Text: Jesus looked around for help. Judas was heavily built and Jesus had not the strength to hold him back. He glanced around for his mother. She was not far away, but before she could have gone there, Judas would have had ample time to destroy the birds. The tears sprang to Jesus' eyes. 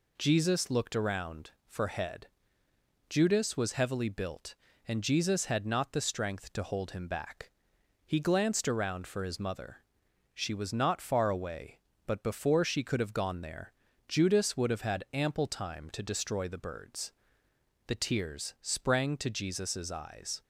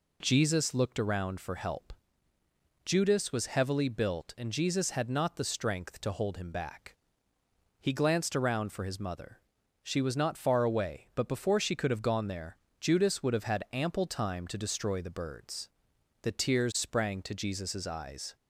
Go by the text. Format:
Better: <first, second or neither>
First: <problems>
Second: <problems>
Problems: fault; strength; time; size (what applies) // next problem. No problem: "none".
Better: second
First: says "head" for "help"; at 1.8 s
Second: none